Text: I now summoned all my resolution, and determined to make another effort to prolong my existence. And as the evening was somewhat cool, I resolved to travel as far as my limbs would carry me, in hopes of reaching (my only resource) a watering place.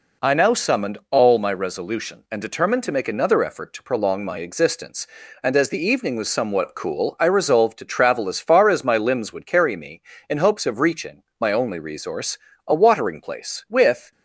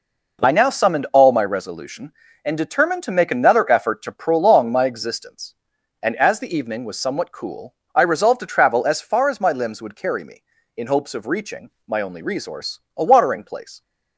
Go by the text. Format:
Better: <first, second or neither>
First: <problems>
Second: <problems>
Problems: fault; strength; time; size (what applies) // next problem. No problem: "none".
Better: second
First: goes on to say "With"; slight; from 13.6 s on; 0.42 s long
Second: none